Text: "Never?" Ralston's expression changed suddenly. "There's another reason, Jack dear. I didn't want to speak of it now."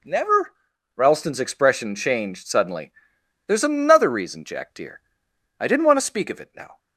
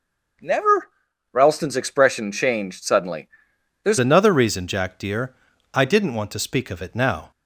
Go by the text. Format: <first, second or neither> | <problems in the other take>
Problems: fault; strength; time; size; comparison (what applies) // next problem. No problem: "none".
first | changes voice at "another"; from 3.9 s on; 3.4 s long